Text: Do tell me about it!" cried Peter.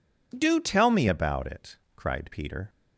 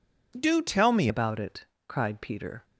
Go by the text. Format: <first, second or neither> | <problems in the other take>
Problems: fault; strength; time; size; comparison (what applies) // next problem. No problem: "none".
first | changes voice at "about"; from 1.0 s on; 1.6 s long